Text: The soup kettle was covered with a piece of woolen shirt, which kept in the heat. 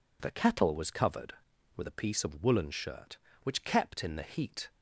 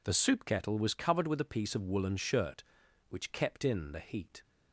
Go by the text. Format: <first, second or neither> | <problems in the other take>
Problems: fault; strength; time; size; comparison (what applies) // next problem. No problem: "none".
second | skips "soup"; at 0.3 s